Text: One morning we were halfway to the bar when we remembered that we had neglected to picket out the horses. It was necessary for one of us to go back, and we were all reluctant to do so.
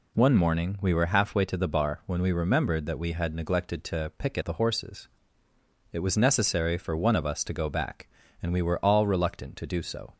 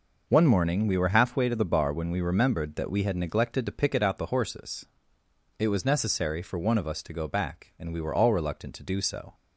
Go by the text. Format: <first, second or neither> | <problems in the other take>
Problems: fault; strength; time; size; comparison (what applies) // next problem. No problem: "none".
second | skips "out"; at 4.4 s